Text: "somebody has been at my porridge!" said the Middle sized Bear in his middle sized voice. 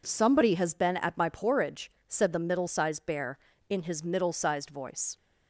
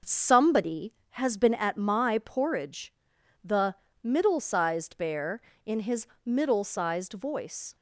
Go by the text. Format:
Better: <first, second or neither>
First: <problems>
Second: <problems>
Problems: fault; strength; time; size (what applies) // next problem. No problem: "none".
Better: first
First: none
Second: skips "said"; at 3.1 s // pauses between "the" and "Middle"; slight; at 3.7 s; 0.28 s long // pauses between "his" and "middle"; slight; at 6.0 s; 0.16 s long